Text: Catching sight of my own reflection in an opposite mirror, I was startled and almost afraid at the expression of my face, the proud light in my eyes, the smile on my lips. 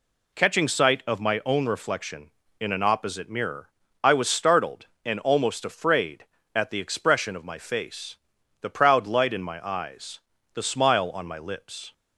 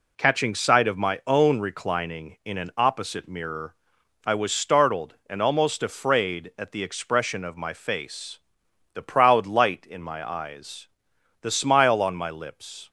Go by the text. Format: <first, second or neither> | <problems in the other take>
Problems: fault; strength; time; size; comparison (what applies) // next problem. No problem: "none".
first | says "reclining" for "reflection"; at 1.5 s